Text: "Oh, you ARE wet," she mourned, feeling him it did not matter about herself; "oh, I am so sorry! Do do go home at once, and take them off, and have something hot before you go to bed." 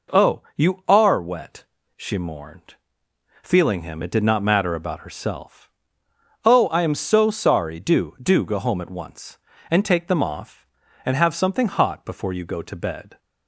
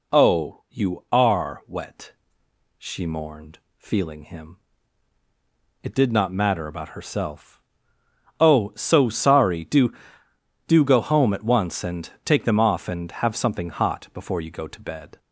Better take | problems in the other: first | pauses between "him" and "it"; at 4.5 s; 1.2 s long // skips "I am"; at 8.7 s // pauses between "and" and "take"; slight; at 12.0 s; 0.16 s long

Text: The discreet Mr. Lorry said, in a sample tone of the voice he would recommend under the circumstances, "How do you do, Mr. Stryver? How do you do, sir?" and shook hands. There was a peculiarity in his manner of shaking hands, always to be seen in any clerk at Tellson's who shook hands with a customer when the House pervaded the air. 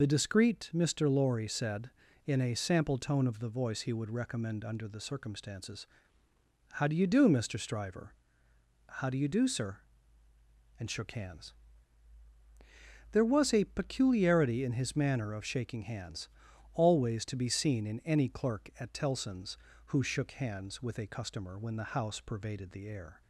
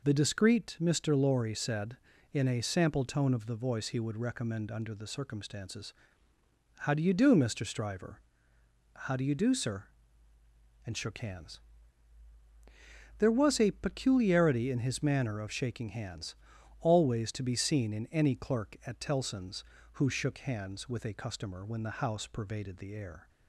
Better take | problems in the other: second | loses the start of "The"; at 0.0 s; 25 ms

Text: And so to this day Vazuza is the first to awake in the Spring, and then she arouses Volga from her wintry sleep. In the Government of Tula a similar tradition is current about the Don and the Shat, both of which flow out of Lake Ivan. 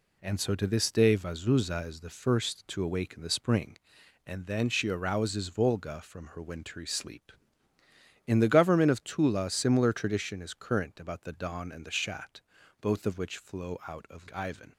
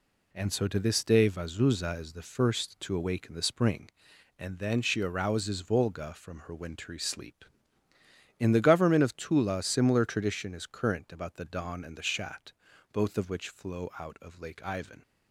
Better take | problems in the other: second | skips "Lake"; at 14.3 s

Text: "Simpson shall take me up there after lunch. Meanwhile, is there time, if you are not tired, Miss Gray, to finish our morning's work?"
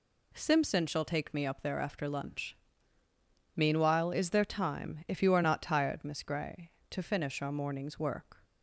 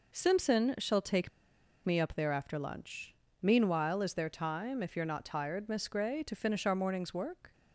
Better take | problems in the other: first | pauses between "take" and "me"; noticeable; at 1.2 s; 0.56 s long

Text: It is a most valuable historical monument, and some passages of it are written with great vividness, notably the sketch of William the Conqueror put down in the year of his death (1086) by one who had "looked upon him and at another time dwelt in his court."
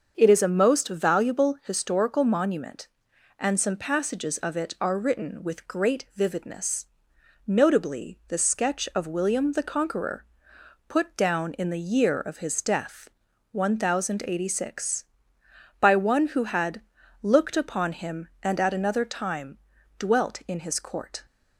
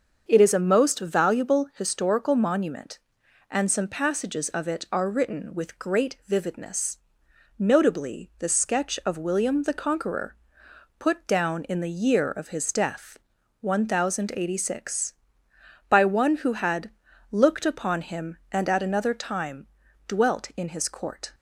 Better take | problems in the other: neither | starts louder than the rest; the same in both // pauses between "Conqueror" and "put"; noticeable; the same in both // pauses between "had" and "looked"; the same in both // pauses between "time" and "dwelt"; the same in both

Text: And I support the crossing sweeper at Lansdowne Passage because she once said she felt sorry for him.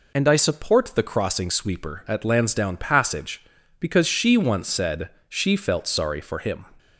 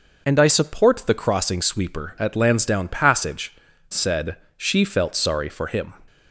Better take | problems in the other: first | skips "because she once"; at 3.7 s // pauses between "said" and "she"; slight; at 4.3 s; 0.20 s long; slight in the first

